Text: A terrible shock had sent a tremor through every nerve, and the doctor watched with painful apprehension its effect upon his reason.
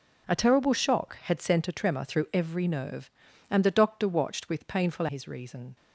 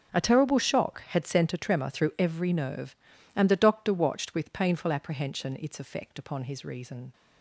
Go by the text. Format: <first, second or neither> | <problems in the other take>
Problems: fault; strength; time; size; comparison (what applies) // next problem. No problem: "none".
second | skips "apprehension its effect upon"; at 5.0 s